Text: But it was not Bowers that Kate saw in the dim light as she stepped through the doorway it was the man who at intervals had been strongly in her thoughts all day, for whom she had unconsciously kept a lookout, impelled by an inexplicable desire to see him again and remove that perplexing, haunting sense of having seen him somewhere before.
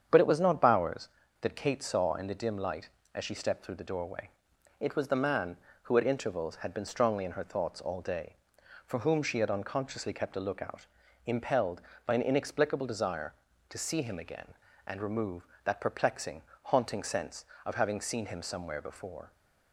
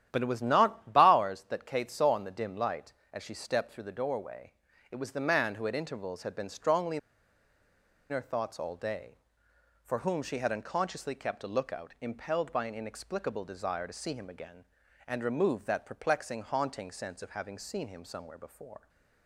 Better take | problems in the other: first | starts louder than the rest; strong; until 1.1 s; 10.5 dB; strong in the first // pauses between "doorway" and "it"; at 4.5 s; 0.40 s long; noticeable in the first // pauses between "in" and "her"; at 6.9 s; 1.1 s long

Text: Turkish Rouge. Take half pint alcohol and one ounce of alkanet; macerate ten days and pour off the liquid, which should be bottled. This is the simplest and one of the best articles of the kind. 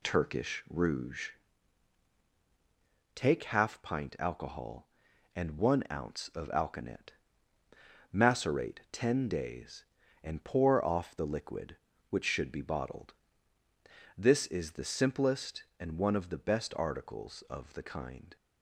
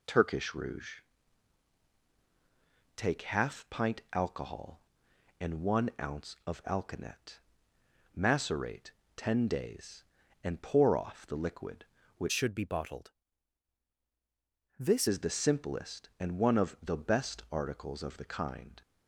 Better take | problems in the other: first | pauses between "macerate" and "ten"; slight; at 8.9 s; 0.24 s long // changes voice from "should" to "This"; from 12.3 to 15.0 s; 2.7 s long

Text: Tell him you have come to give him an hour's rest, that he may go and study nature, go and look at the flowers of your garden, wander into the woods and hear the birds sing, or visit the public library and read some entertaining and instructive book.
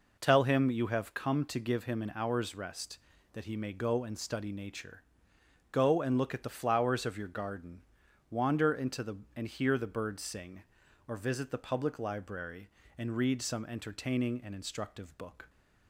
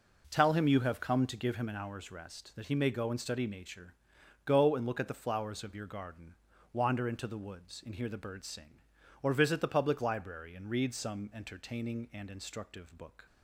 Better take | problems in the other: second | skips "woods"; at 9.2 s

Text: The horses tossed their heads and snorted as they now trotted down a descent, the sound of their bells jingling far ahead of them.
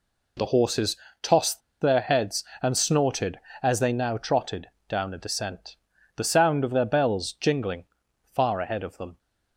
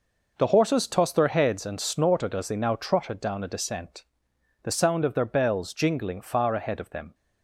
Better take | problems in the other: second | pauses between "horses" and "tossed"; slight; at 0.9 s; 0.24 s long // pauses between "tossed" and "their"; slight; at 1.6 s; 0.21 s long // pauses between "trotted" and "down"; slight; at 4.6 s; 0.20 s long // pauses between "jingling" and "far"; noticeable; at 7.8 s; 0.50 s long

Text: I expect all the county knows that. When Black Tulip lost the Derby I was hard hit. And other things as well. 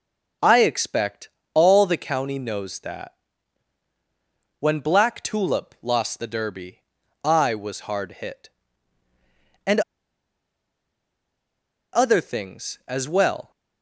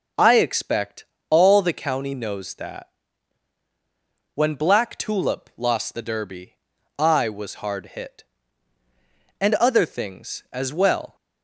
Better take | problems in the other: second | starts louder than the rest; noticeable; until 1.6 s; 6 dB; noticeable in the second // pauses between "expect" and "all"; slight; at 1.2 s; 0.26 s long; slight in the second // pauses between "Derby" and "I"; at 6.8 s; 0.44 s long; also in the second // pauses between "And" and "other"; strong; at 9.7 s; 2.1 s long

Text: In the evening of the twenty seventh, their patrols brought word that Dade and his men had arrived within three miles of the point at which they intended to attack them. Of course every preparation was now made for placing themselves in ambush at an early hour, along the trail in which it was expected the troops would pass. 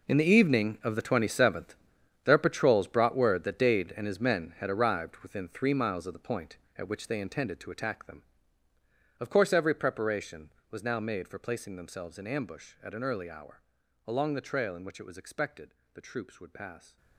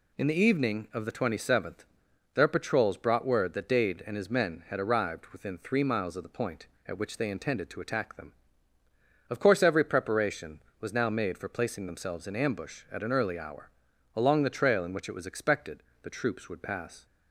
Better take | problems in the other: second | gets quieter; strong; throughout; 14 dB // pauses between "expected" and "the"; slight; at 15.7 s; 0.22 s long; slight in the second

